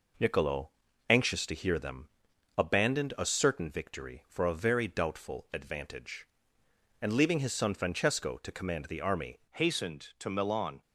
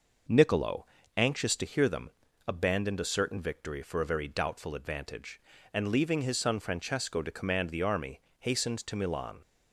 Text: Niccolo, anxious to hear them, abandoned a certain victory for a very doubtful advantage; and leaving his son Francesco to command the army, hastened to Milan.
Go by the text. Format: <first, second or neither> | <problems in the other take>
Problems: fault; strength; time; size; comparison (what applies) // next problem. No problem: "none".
second | changes voice at "hastened"; from 9.5 s on; 1.3 s long